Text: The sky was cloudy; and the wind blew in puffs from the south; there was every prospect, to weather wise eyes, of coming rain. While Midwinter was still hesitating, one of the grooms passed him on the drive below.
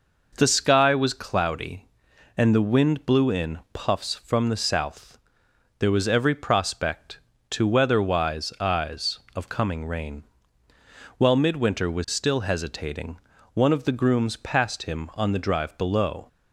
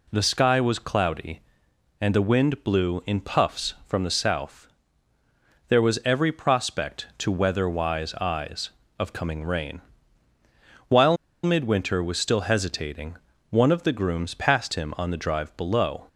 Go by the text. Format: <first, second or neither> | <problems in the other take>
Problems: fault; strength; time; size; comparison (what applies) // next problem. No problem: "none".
first | pauses between "While" and "Midwinter"; slight; at 11.1 s; 0.29 s long